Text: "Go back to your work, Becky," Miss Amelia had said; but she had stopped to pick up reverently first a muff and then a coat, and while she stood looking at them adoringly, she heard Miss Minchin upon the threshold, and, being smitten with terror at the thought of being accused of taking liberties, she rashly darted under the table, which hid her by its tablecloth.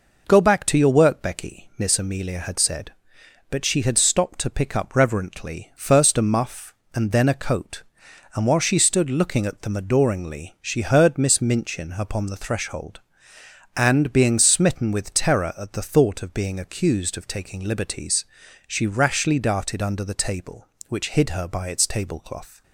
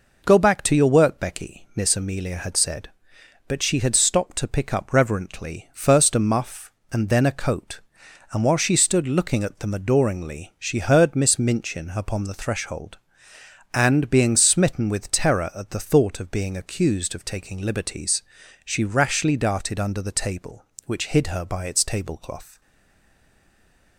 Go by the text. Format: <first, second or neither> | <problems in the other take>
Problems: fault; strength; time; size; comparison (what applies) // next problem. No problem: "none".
first | stays silent after the last word; noticeable; from 22.6 s on; 1.3 s long